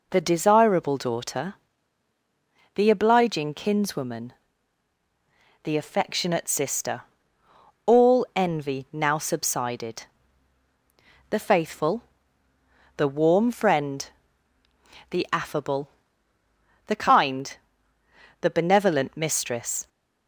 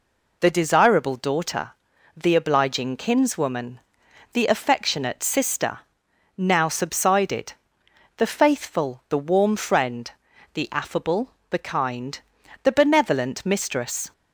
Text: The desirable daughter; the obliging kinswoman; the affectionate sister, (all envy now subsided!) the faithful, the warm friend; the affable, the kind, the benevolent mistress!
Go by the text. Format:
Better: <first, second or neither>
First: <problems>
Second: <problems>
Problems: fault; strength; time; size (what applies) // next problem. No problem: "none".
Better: first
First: none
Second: skips "all envy"; at 6.0 s